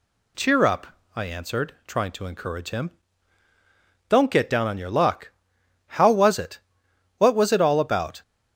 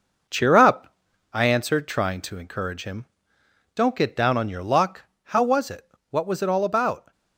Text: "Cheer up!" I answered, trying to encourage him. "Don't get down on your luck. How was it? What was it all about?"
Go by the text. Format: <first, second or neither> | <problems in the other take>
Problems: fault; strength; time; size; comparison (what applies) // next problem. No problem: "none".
first | gets quieter; noticeable; throughout; 4.5 dB